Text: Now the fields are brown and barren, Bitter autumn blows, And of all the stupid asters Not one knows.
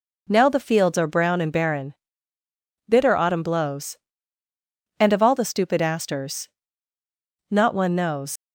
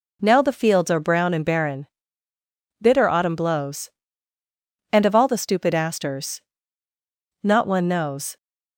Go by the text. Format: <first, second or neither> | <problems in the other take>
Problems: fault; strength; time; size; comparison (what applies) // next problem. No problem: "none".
second | pauses between "asters" and "Not"; at 6.4 s; 1.0 s long; also in the second // leaves "knows" unfinished; at 8.3 s; 80 ms